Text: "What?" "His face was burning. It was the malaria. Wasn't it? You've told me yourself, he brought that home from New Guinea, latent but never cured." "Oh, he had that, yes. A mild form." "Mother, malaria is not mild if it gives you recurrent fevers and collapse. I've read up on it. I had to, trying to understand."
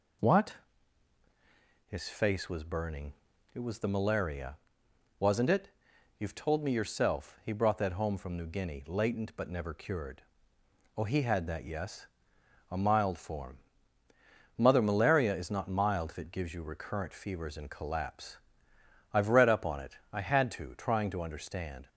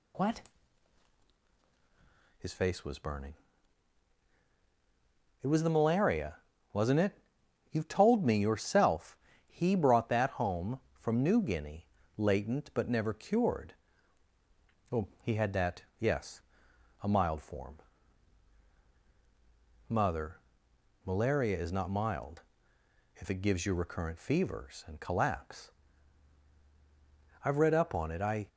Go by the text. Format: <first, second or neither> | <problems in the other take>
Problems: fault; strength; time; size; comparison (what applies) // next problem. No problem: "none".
first | pauses between "mild" and "if"; noticeable; at 22.4 s; 0.74 s long // stops before "had to trying to understand"; at 28.4 s